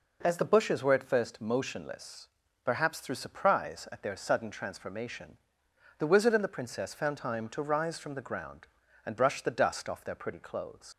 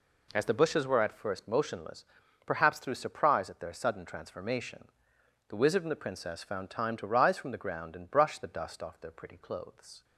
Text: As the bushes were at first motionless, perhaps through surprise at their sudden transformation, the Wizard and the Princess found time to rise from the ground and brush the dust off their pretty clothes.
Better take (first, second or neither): second